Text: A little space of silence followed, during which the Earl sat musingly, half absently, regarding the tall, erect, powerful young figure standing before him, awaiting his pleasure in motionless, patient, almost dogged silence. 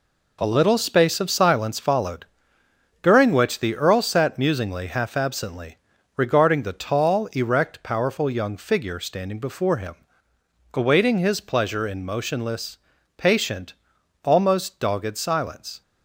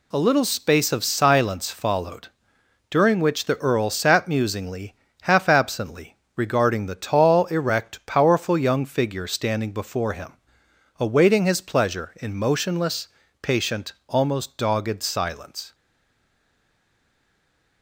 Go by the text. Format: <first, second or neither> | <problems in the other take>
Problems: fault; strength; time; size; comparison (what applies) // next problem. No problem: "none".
first | stays silent after the last word; noticeable; from 15.7 s on; 2.1 s long